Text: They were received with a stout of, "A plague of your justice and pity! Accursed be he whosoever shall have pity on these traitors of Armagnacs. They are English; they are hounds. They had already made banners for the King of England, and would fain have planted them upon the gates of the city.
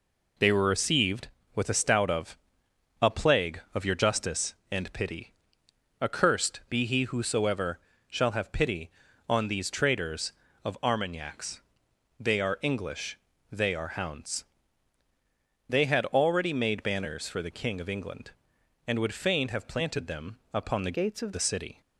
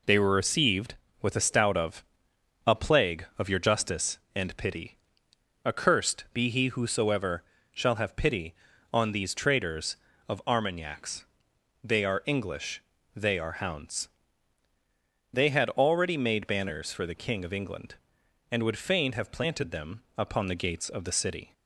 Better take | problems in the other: second | pauses between "whosoever" and "shall"; slight; at 7.7 s; 0.28 s long; slight in the second // changes voice from "gates" to "of"; from 20.9 to 21.3 s; 0.4 s long

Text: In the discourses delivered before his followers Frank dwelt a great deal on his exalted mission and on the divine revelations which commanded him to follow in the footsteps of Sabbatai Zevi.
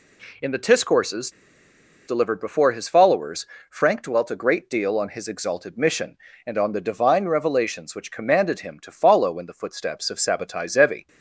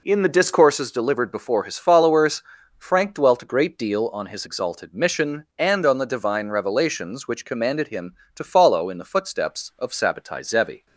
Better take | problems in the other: second | pauses between "discourses" and "delivered"; noticeable; at 1.3 s; 0.76 s long // pauses between "followers" and "Frank"; slight; at 3.4 s; 0.24 s long; slight in the second

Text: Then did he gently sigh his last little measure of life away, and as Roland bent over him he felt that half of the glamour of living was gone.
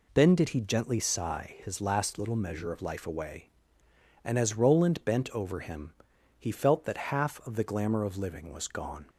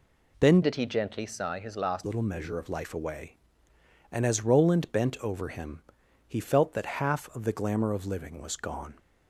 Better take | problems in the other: first | changes voice from "did" to "last"; from 0.6 to 2.0 s; 1.4 s long // pauses between "him" and "he"; noticeable; at 5.8 s; 0.46 s long; noticeable in the first

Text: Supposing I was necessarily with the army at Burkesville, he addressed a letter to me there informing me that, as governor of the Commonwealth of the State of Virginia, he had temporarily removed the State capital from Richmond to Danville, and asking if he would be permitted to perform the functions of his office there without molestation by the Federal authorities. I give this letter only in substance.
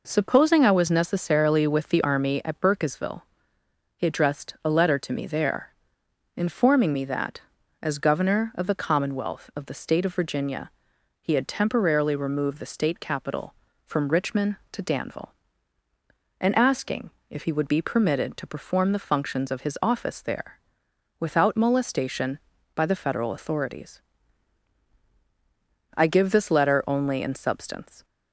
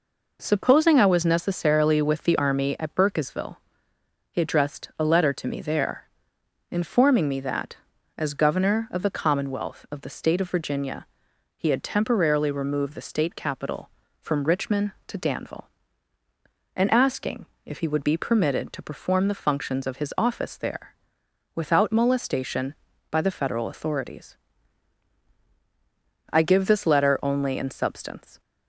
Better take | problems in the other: neither | pauses between "there" and "informing"; noticeable; the same in both // pauses between "asking" and "if"; slight; the same in both // pauses between "there" and "without"; noticeable; the same in both

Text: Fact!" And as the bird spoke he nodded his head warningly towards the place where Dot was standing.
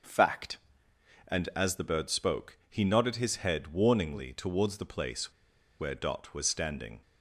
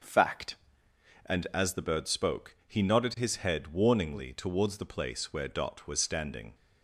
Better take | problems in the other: second | starts louder than the rest; until 1.8 s; 6.5 dB; also in the second // pauses between "place" and "where"; noticeable; at 5.3 s; 0.47 s long

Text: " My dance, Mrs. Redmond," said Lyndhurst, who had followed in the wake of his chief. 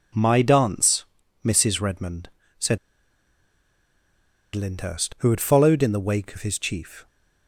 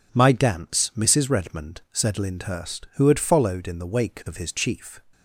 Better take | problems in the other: second | pauses between "said" and "Lyndhurst"; strong; at 2.7 s; 1.7 s long

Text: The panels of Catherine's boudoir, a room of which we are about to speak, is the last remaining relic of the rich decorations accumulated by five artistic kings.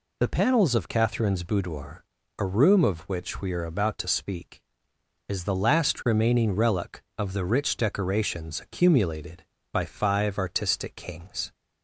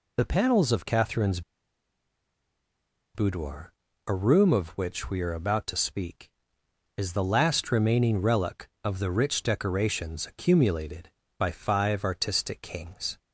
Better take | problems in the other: first | pauses between "Catherine's" and "boudoir"; strong; at 1.4 s; 1.7 s long

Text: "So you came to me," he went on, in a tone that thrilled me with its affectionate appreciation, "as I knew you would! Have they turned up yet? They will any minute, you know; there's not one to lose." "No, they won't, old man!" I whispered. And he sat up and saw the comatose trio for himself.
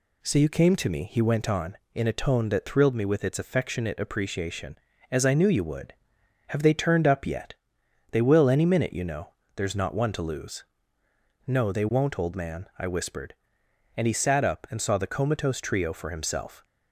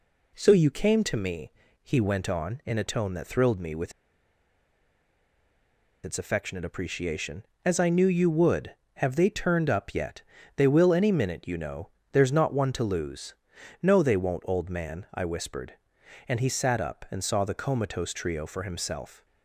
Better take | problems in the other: first | pauses between "with" and "its"; strong; at 3.9 s; 2.1 s long

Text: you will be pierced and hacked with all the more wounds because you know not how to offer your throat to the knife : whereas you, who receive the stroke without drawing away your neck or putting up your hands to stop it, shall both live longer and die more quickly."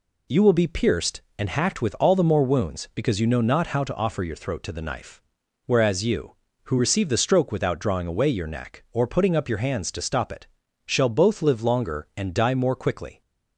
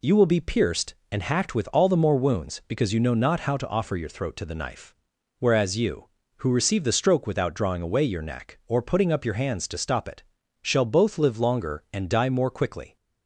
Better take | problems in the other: neither | none

